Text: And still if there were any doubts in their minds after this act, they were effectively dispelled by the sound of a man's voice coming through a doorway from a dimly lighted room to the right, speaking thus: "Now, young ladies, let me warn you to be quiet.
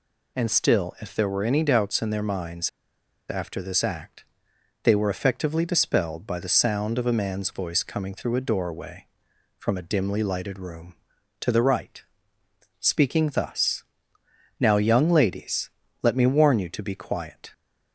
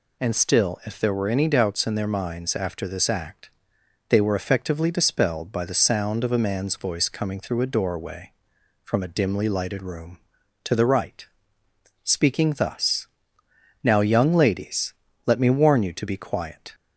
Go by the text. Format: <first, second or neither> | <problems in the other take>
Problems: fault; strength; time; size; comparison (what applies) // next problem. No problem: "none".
second | pauses between "minds" and "after"; noticeable; at 2.6 s; 0.60 s long